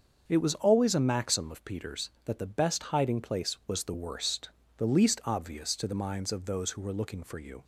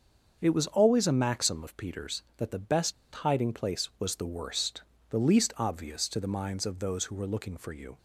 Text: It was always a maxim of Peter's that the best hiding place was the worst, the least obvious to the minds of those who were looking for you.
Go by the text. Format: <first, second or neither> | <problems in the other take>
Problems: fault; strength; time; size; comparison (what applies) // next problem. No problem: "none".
first | starts louder than the rest; until 1.4 s; 6.5 dB; also in the first // pauses between "best" and "hiding"; slight; at 2.9 s; 0.22 s long